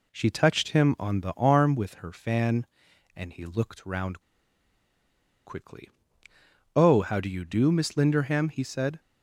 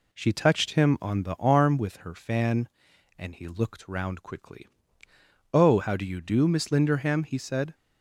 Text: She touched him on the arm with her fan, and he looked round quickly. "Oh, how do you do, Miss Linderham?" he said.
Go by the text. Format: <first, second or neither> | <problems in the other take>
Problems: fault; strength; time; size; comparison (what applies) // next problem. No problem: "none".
second | pauses between "round" and "quickly"; strong; at 4.1 s; 1.2 s long